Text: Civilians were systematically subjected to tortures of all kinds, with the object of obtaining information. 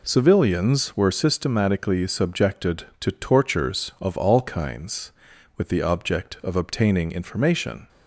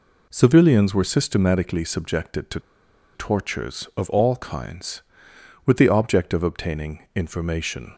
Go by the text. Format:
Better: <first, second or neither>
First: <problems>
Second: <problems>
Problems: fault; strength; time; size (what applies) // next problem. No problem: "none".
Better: first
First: none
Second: pauses between "to" and "tortures"; noticeable; at 2.5 s; 0.54 s long